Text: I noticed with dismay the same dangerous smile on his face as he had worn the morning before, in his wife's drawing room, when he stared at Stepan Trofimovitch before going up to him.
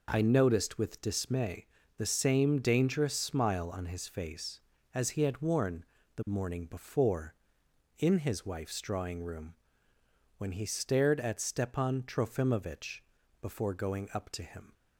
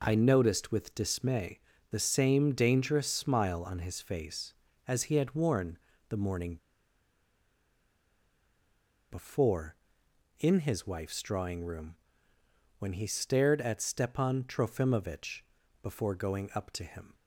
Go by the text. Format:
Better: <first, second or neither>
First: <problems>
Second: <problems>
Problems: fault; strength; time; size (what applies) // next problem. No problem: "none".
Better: first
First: pauses between "dismay" and "the"; slight; at 1.6 s; 0.30 s long // pauses between "worn" and "the"; slight; at 5.8 s; 0.30 s long // pauses between "Trofimovitch" and "before"; at 13.0 s; 0.40 s long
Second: pauses between "dismay" and "the"; slight; at 1.6 s; 0.30 s long // pauses between "worn" and "the"; slight; at 5.7 s; 0.30 s long // pauses between "morning" and "before"; strong; at 6.5 s; 2.5 s long // pauses between "Trofimovitch" and "before"; at 15.4 s; 0.40 s long